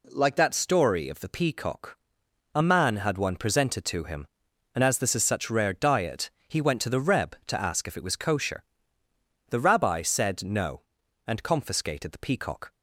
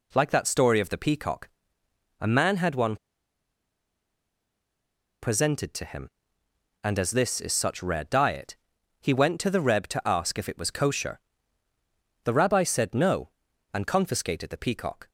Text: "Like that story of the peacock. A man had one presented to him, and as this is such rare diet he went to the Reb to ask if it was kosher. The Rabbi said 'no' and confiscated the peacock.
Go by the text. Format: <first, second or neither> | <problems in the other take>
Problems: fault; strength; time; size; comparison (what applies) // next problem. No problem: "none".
first | pauses between "one" and "presented"; strong; at 2.9 s; 2.2 s long // pauses between "diet" and "he"; at 8.5 s; 0.42 s long; slight in the first